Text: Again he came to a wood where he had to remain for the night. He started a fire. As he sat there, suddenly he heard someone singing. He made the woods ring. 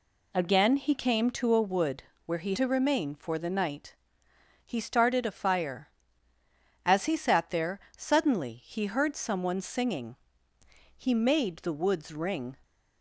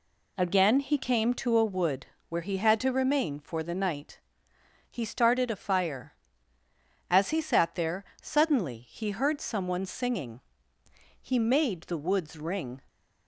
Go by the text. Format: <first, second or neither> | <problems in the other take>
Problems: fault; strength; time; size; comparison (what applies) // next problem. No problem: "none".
second | pauses between "wood" and "where"; slight; at 2.0 s; 0.22 s long; slight in the second // skips "had"; at 2.5 s